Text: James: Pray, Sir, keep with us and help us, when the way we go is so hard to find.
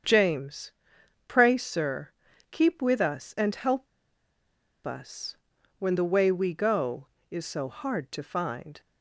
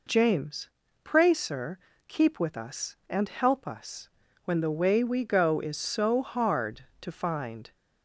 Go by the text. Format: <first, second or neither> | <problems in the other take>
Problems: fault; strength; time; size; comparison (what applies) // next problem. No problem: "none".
second | starts louder than the rest; strong; until 1.6 s; 7.5 dB // pauses between "help" and "us"; at 3.8 s; 0.99 s long